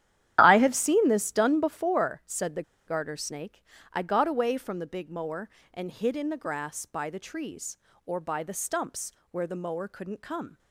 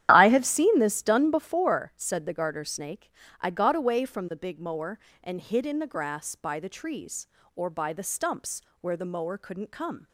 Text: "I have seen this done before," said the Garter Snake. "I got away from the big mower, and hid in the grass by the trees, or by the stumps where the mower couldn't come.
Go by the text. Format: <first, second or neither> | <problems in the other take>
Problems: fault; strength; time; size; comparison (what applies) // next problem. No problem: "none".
second | starts louder than the rest; strong; until 1.4 s; 11 dB; strong in the second // pauses between "the" and "Garter"; slight; at 2.6 s; 0.25 s long // pauses between "stumps" and "where"; slight; at 9.1 s; 0.22 s long; slight in the second